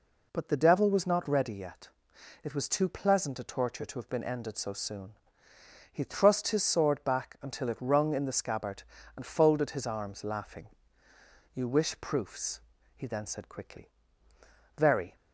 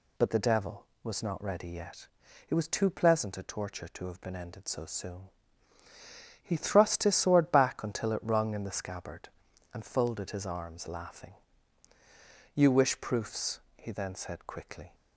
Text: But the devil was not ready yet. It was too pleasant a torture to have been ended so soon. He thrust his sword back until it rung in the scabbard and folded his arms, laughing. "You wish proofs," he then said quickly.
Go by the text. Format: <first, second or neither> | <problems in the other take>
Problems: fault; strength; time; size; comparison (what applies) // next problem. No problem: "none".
second | goes on to say "Very"; slight; from 14.7 s on; 0.38 s long